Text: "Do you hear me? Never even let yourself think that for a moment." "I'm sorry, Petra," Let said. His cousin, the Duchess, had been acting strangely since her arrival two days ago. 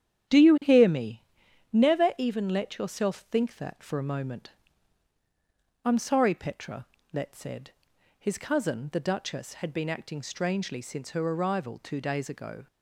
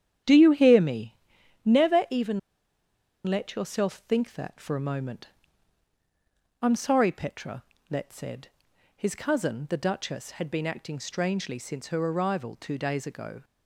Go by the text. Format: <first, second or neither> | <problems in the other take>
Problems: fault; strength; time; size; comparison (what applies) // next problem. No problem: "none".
first | starts louder than the rest; strong; until 1.7 s; 10 dB; strong in the first // pauses between "even" and "let"; noticeable; at 2.3 s; 0.86 s long